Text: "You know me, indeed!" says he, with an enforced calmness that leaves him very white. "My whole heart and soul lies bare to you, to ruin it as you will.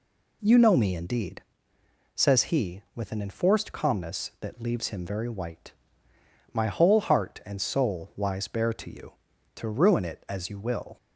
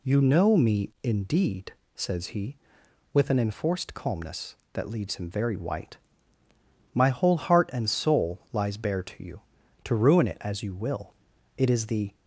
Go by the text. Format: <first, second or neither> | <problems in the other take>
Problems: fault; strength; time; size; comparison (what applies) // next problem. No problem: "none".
first | goes on to say "It is the"; from 11.5 s on; 0.56 s long